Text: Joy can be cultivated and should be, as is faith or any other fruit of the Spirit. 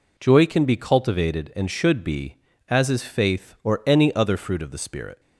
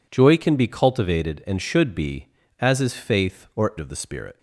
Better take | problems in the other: first | skips "any other fruit"; at 3.7 s

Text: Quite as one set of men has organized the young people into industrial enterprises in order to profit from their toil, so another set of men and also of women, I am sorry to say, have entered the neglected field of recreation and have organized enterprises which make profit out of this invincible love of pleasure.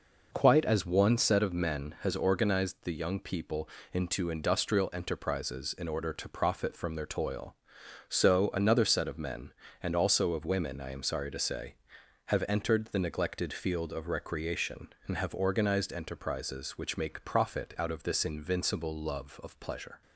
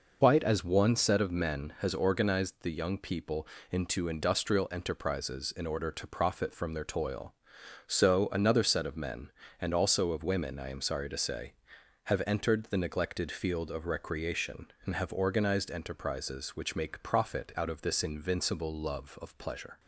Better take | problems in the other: first | loses the start of "Quite"; at 0.2 s; 95 ms // pauses between "people" and "into"; slight; at 3.4 s; 0.24 s long; slight in the first

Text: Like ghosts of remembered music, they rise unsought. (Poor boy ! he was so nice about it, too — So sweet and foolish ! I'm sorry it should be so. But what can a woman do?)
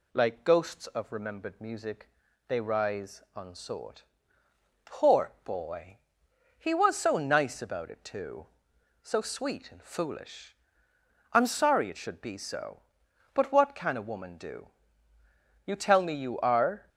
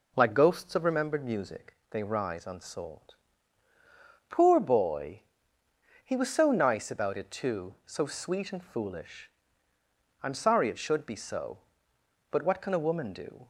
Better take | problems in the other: second | goes on to say "You tell me you are"; noticeable; from 15.6 s on; 1.2 s long

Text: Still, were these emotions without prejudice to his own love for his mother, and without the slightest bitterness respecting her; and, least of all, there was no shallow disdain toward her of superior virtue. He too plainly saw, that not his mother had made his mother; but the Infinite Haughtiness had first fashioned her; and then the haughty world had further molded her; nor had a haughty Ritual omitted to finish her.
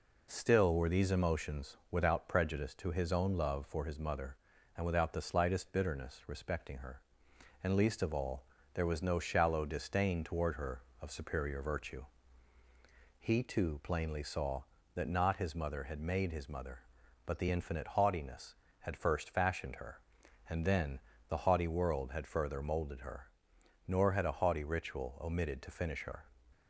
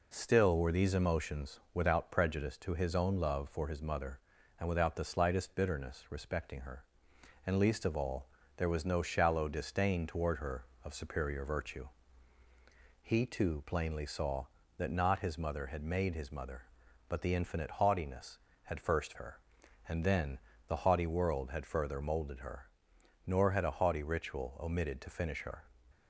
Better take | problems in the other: first | skips "fashioned"; at 19.1 s // pauses between "then" and "the"; slight; at 20.3 s; 0.30 s long; slight in the first

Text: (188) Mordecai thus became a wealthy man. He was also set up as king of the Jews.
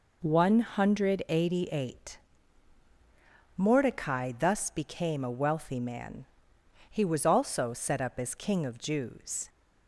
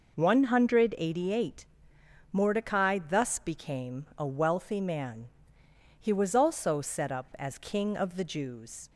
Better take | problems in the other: second | skips "the"; at 8.7 s

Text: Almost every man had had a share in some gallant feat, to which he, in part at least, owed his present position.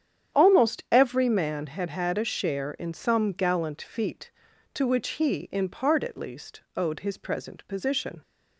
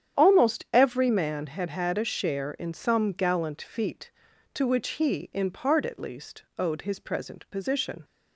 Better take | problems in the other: neither | starts louder than the rest; strong; the same in both

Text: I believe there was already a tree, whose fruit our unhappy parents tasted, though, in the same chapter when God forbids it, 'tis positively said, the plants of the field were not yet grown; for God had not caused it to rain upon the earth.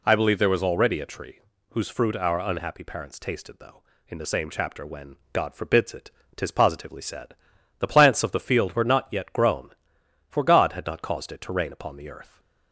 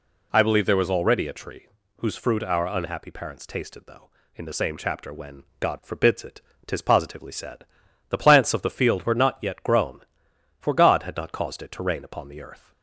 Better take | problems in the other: neither | pauses between "when" and "God"; slight; the same in both

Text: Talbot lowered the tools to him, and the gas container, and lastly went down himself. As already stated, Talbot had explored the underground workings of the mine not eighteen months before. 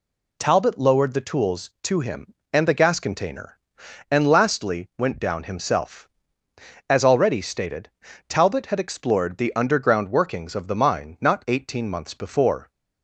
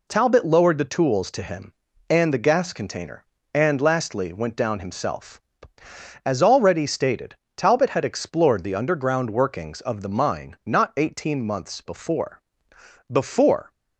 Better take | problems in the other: first | says "before" twice; at 13.1 s

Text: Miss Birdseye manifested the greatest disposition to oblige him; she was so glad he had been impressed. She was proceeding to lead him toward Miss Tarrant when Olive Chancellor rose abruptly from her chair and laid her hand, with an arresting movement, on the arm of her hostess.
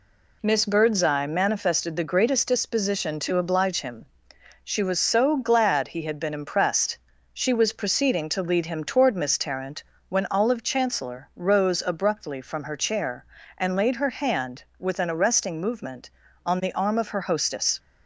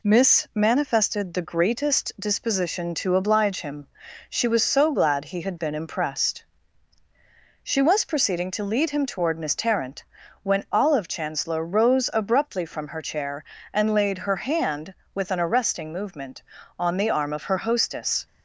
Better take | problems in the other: first | skips "Birdseye"; at 0.5 s // pauses between "Tarrant" and "when"; at 10.0 s; 0.40 s long; slight in the first

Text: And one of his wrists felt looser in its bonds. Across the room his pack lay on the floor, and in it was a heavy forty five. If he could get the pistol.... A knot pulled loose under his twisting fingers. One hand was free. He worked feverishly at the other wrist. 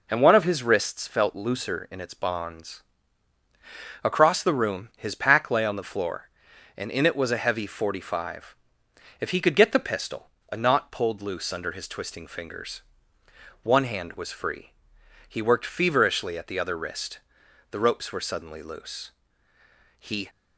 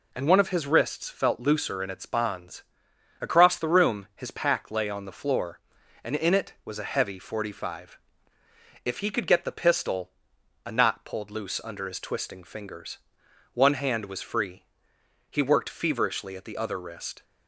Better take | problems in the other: second | goes on to say "The ropes were suddenly loose He"; strong; from 17.7 s on; 2.5 s long

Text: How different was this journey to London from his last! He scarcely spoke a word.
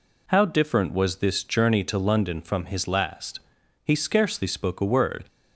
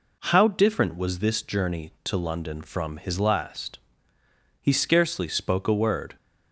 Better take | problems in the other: neither | none

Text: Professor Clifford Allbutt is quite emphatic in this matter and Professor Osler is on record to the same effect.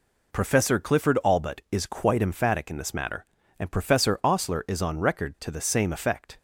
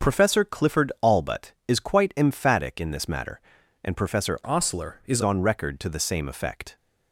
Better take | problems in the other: first | starts louder than the rest; until 1.1 s; 6.5 dB // changes voice from "Osler" to "is"; from 4.4 to 5.2 s; 0.8 s long

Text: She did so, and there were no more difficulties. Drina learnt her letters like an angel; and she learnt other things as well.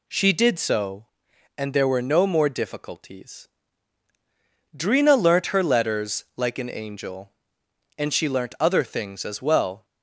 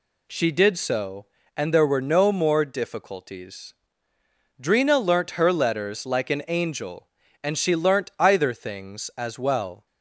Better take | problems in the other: first | says "either" for "other"; at 8.1 s

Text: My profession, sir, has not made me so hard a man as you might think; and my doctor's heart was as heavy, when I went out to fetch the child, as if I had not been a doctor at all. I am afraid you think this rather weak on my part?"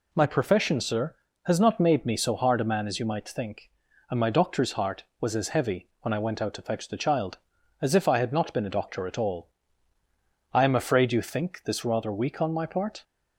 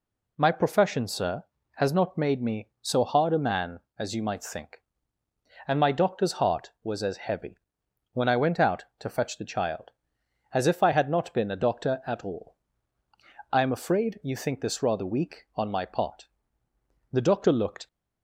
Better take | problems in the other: first | goes on to say "The doctor looked"; noticeable; from 17.1 s on; 0.76 s long

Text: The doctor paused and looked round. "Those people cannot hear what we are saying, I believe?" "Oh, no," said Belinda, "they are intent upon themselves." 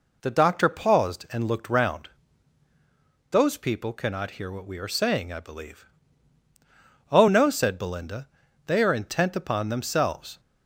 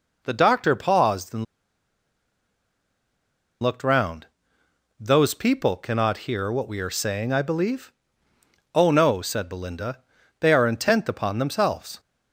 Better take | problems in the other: first | pauses between "and" and "looked"; strong; at 1.4 s; 2.1 s long

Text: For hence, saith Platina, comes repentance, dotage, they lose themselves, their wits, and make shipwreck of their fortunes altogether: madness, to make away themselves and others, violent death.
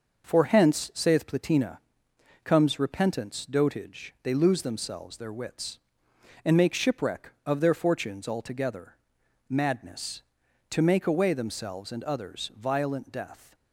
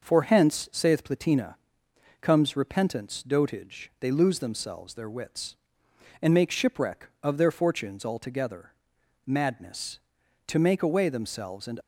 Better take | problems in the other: first | stops before "others violent death"; at 11.8 s

